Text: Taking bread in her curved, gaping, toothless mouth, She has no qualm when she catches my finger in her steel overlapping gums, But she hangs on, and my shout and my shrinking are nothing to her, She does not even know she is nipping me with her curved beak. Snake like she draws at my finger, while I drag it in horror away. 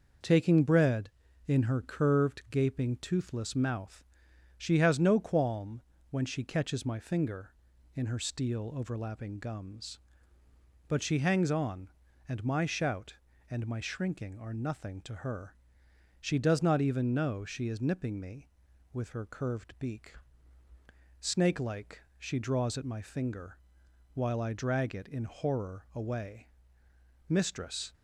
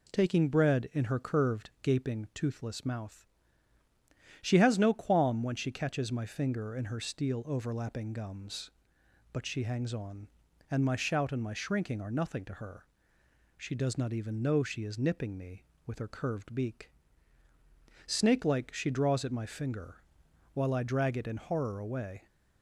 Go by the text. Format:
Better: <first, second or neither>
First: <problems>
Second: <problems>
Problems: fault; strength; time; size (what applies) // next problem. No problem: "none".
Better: second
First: pauses between "qualm" and "when"; slight; at 5.8 s; 0.30 s long // pauses between "like" and "she"; slight; at 22.0 s; 0.16 s long // goes on to say "Mistress"; noticeable; from 27.2 s on; 0.66 s long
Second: none